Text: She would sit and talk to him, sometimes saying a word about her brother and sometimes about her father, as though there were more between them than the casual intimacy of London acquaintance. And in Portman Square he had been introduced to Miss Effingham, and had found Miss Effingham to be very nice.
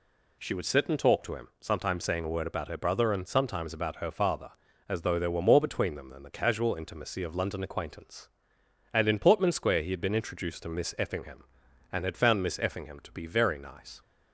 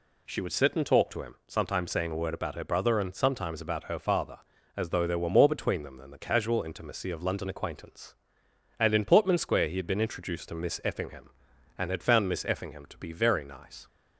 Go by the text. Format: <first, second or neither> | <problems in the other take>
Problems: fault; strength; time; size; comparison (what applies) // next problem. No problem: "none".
neither | none